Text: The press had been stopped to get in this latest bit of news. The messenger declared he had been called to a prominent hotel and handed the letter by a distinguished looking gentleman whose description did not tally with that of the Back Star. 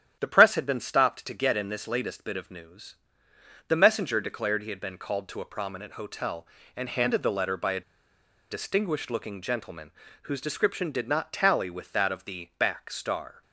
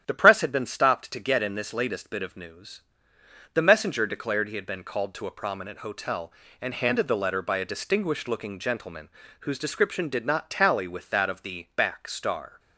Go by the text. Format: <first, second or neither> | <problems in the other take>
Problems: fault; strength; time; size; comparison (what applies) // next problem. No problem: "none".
second | starts louder than the rest; strong; until 1.2 s; 10 dB; strong in the second // pauses between "a" and "distinguished"; noticeable; at 7.8 s; 0.69 s long // pauses between "gentleman" and "whose"; slight; at 9.9 s; 0.32 s long; slight in the second